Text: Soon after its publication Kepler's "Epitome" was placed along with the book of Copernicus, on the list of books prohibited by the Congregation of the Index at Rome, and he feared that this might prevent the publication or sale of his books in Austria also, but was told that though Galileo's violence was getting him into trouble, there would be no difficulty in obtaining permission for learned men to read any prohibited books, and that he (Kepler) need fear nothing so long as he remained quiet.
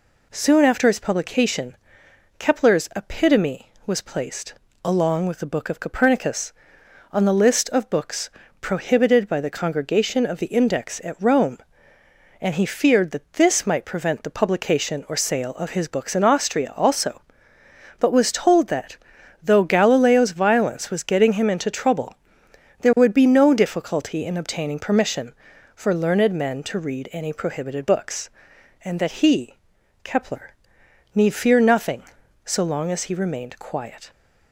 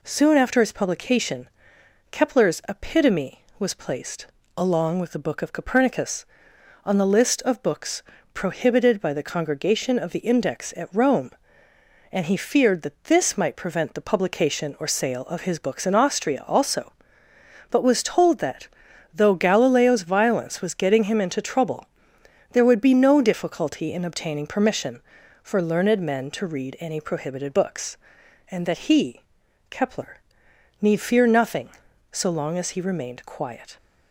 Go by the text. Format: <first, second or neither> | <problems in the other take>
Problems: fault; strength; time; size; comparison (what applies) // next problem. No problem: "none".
neither | pauses between "publication" and "Kepler's"; noticeable; the same in both // pauses between "placed" and "along"; slight; the same in both // pauses between "books" and "prohibited"; slight; the same in both // pauses between "that" and "though"; noticeable; the same in both